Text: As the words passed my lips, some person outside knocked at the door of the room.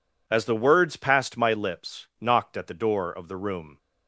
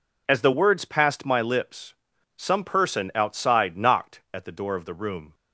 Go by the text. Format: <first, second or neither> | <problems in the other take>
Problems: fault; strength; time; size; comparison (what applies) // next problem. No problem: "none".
second | skips "some person outside"; at 2.1 s